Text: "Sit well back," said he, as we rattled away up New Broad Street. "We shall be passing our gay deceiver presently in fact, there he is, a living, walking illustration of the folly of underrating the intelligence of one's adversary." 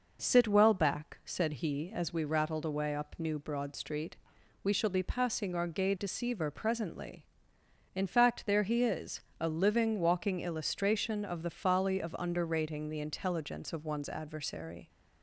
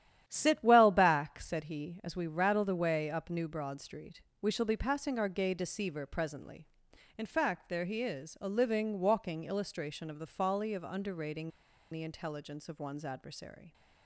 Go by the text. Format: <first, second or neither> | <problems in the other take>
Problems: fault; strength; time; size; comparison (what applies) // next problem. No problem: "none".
first | starts louder than the rest; strong; until 1.2 s; 11.5 dB // pauses between "underrating" and "the"; at 11.5 s; 0.41 s long